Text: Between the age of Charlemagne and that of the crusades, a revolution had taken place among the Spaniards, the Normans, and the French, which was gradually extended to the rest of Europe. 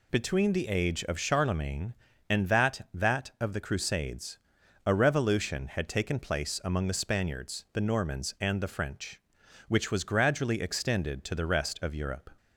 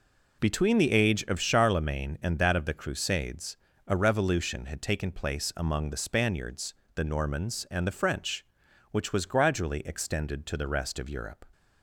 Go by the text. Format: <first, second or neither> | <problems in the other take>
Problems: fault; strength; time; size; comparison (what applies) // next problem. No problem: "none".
second | says "that" twice; at 2.9 s